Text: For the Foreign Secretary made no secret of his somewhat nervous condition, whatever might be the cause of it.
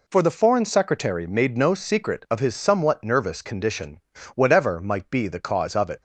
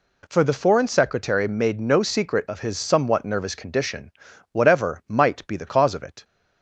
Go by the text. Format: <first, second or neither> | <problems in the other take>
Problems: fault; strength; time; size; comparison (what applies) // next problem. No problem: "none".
neither | none